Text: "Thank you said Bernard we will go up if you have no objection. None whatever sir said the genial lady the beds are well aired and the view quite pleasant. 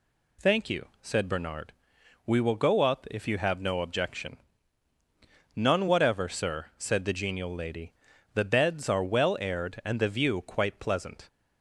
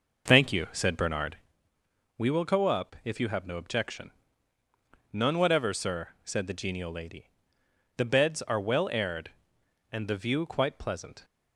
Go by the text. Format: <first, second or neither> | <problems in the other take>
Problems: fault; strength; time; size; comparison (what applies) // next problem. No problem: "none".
first | starts louder than the rest; noticeable; until 1.6 s; 5.5 dB // pauses between "Bernard" and "we"; noticeable; at 1.3 s; 0.82 s long; noticeable in the first // pauses between "lady" and "the"; noticeable; at 7.3 s; 0.66 s long; also in the first